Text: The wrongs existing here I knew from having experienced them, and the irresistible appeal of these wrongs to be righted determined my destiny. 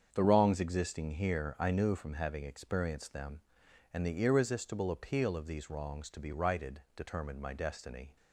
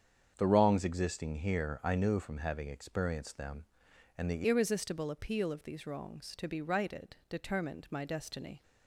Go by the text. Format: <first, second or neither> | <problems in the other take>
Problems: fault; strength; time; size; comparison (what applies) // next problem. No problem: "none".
first | starts louder than the rest; strong; until 1.3 s; 7.5 dB; strong in the first // changes voice at "irresistible"; from 4.4 s on; 4.2 s long